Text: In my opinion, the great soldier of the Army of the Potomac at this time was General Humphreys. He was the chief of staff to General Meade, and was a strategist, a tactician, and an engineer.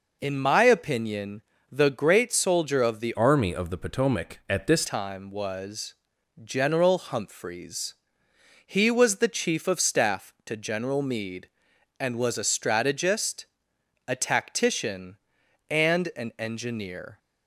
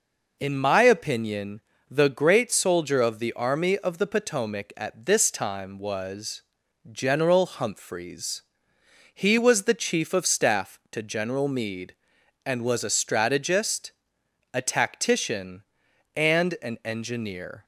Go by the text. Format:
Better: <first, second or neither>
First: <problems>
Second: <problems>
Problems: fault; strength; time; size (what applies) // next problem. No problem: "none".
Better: second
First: changes voice from "Army" to "this"; from 3.1 to 4.8 s; 1.7 s long // pauses between "was" and "General"; noticeable; at 5.9 s; 0.50 s long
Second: pauses between "was" and "General"; noticeable; at 6.4 s; 0.50 s long